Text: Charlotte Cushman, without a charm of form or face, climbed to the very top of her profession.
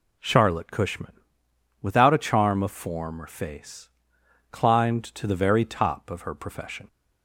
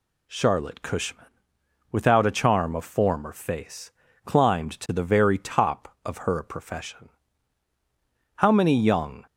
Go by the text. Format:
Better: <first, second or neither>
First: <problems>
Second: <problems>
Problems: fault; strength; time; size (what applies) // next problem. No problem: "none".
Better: first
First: none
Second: goes on to say "How many young"; noticeable; from 8.3 s on; 0.90 s long